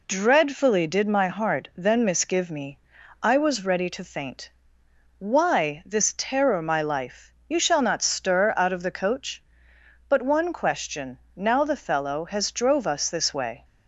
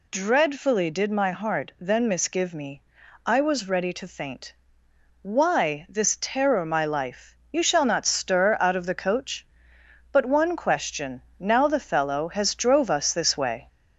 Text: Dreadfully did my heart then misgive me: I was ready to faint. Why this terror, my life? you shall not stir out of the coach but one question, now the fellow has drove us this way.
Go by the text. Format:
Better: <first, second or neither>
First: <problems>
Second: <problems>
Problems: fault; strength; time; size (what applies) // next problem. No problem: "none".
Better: first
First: none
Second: gets louder; slight; throughout; 2 dB